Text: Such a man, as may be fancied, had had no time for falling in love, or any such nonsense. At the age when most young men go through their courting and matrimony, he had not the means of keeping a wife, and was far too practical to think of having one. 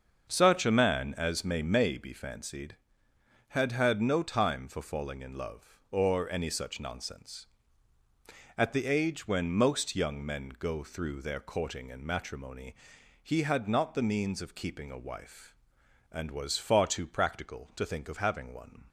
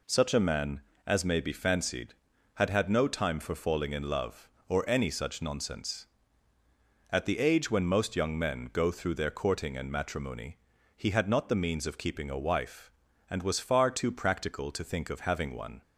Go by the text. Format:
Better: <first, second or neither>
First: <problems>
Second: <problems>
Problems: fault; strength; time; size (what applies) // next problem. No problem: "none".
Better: second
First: starts louder than the rest; until 1.3 s; 6.5 dB // says "may" twice; at 1.6 s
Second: none